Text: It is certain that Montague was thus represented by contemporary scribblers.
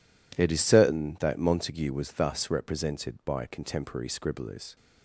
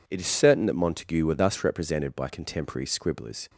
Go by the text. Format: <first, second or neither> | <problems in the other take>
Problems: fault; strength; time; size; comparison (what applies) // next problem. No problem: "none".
first | says "were" for "was"; at 1.2 s